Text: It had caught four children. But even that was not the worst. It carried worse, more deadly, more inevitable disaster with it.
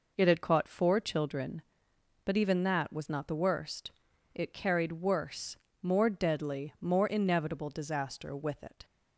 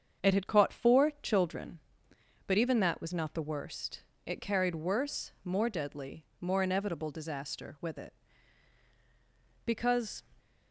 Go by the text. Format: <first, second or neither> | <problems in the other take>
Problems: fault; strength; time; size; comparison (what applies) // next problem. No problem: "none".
first | starts louder than the rest; strong; until 1.3 s; 7 dB // goes on to say "Because"; from 9.6 s on; 0.56 s long